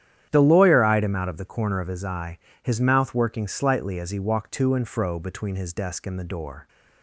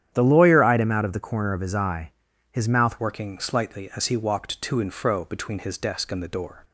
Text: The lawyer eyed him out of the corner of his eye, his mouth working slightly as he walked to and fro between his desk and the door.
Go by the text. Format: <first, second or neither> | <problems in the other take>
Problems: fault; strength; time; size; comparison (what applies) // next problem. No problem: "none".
first | starts louder than the rest; strong; until 1.1 s; 10 dB; strong in the first // changes voice at "working"; from 2.9 s on; 3.7 s long